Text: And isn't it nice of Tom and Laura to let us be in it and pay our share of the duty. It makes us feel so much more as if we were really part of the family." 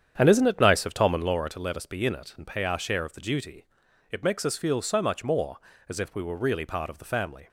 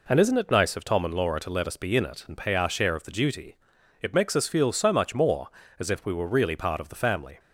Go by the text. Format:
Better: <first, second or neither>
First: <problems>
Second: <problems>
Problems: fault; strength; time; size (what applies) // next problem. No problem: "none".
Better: second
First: starts louder than the rest; strong; until 1.5 s; 8.5 dB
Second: none